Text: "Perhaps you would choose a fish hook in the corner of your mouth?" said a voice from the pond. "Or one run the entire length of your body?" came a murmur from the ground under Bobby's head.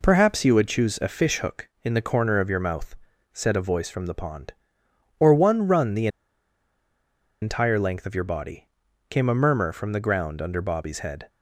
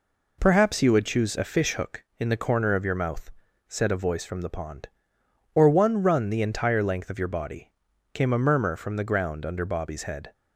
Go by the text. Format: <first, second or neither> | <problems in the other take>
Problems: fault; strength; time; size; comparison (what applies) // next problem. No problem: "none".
second | pauses between "the" and "entire"; strong; at 6.0 s; 1.3 s long